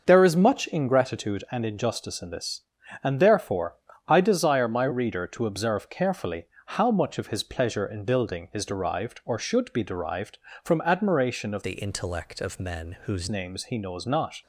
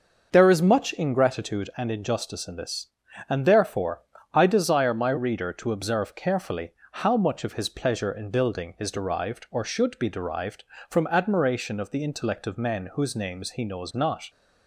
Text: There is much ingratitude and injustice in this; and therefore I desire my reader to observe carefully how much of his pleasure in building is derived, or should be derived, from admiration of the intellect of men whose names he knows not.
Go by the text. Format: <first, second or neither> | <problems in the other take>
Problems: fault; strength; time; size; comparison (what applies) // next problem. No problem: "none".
second | starts louder than the rest; noticeable; until 1.0 s; 6 dB; noticeable in the second // pauses between "therefore" and "I"; slight; at 3.7 s; 0.32 s long; slight in the second // pauses between "carefully" and "how"; slight; at 6.4 s; 0.20 s long; slight in the second // changes voice from "the" to "whose"; from 11.6 to 13.2 s; 1.6 s long